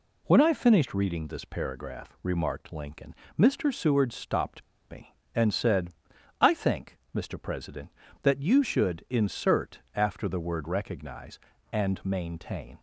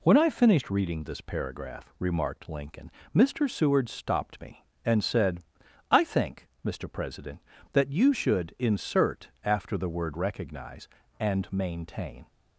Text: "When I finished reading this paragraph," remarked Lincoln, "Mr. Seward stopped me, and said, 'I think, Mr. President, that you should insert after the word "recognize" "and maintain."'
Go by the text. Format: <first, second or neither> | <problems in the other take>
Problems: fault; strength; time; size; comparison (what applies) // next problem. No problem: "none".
second | pauses between "stopped" and "me"; slight; at 4.6 s; 0.27 s long